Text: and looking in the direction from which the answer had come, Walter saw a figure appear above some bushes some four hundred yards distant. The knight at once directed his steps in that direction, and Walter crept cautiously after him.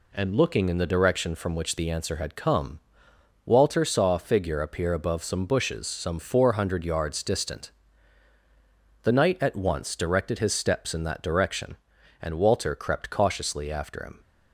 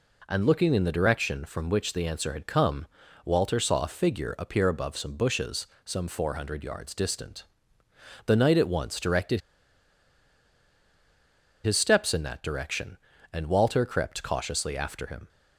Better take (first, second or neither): first